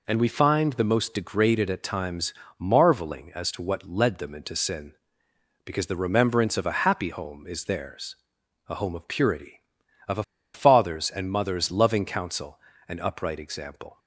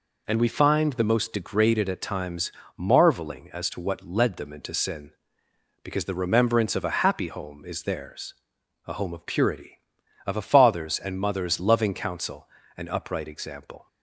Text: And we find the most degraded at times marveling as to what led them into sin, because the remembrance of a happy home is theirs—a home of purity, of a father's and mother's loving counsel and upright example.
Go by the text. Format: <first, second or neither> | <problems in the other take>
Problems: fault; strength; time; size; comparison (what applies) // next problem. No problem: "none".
second | pauses between "times" and "marveling"; slight; at 2.3 s; 0.26 s long; slight in the second // pauses between "a" and "father's"; slight; at 10.2 s; 0.31 s long